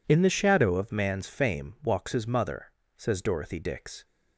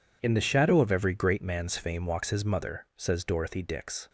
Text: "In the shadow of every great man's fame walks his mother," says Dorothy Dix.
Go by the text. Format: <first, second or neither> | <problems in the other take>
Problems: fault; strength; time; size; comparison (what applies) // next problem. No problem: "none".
second | skips "every great"; at 0.9 s